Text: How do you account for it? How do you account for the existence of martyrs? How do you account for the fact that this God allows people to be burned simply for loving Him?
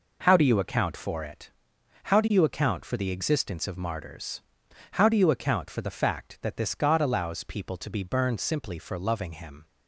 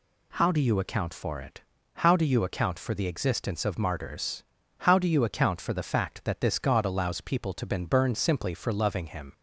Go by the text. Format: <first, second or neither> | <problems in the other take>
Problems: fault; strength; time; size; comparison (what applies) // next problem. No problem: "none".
first | says "been" for "be"; at 7.6 s